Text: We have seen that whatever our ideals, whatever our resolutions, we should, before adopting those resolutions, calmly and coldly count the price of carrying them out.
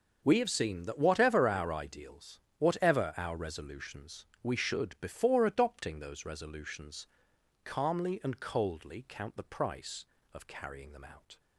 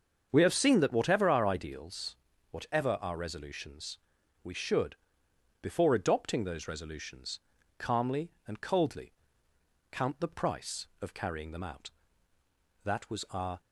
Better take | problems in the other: first | starts louder than the rest; until 1.3 s; 7 dB; noticeable in the first // pauses between "coldly" and "count"; noticeable; at 9.1 s; 0.80 s long // goes on to say "That was our"; noticeable; from 12.8 s on; 0.76 s long

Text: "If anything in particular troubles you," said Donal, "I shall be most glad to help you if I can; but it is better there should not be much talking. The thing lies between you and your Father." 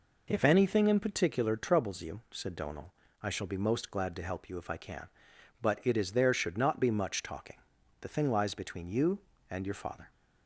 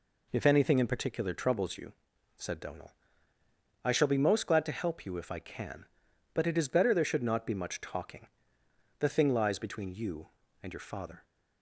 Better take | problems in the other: second | skips "better"; at 6.1 s

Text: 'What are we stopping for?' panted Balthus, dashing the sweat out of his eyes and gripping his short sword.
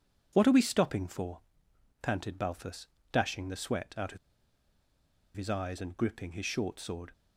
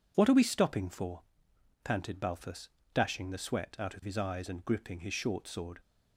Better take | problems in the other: second | pauses between "of" and "his"; at 4.1 s; 1.1 s long

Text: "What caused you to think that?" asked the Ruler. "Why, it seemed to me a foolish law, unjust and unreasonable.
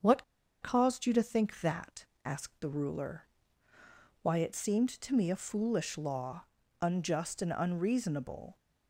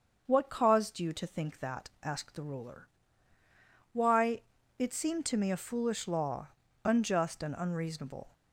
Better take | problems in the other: second | starts louder than the rest; until 1.4 s; 7 dB; also in the second // pauses between "What" and "caused"; at 0.2 s; 0.39 s long

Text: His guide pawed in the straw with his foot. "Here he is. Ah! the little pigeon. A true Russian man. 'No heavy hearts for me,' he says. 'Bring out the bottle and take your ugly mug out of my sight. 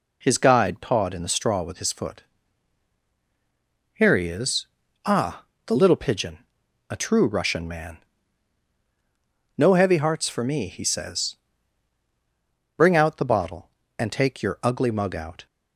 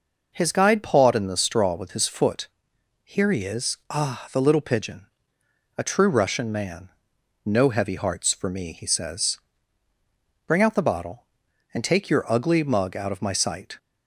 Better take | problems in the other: second | stops before "of my sight"; at 15.4 s

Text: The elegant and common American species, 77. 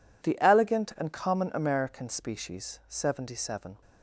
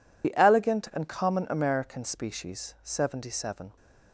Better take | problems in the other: first | loses the start of "The"; at 0.2 s; 55 ms

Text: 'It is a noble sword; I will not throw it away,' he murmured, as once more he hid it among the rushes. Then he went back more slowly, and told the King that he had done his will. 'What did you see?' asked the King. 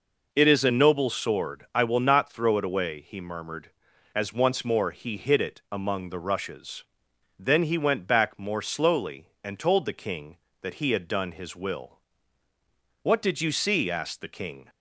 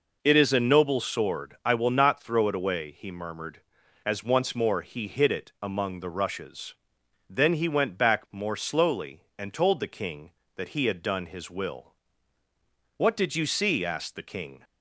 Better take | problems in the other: neither | none

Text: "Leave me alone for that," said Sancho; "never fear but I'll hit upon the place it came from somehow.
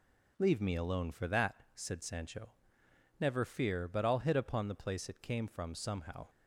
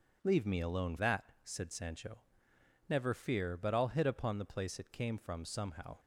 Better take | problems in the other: first | skips "for"; at 0.9 s

